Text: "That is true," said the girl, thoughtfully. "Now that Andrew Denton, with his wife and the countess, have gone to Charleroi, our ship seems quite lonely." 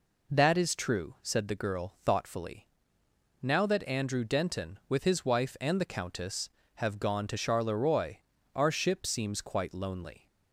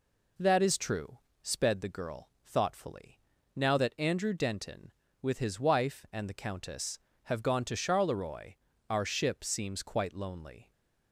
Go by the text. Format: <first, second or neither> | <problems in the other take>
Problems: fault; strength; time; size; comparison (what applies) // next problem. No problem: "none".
first | says "sped" for "said"; at 1.4 s